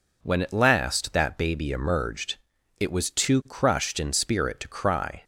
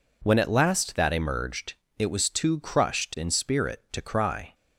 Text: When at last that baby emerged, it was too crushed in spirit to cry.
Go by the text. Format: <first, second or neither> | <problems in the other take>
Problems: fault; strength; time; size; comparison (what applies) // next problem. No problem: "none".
first | skips "baby"; at 1.1 s